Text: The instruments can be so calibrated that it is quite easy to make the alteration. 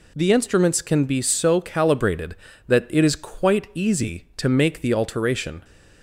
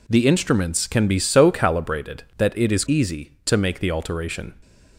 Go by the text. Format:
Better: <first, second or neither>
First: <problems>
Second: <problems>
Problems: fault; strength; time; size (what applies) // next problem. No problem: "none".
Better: first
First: none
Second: skips "quite"; at 2.8 s